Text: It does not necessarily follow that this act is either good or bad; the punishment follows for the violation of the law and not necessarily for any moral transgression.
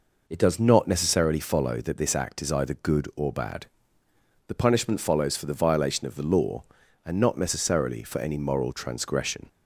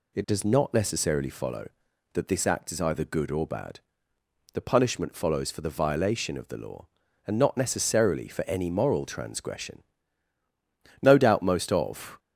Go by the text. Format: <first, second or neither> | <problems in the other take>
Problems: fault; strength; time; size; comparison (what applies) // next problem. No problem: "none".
first | goes on to say "No doubt most of"; noticeable; from 10.9 s on; 1.2 s long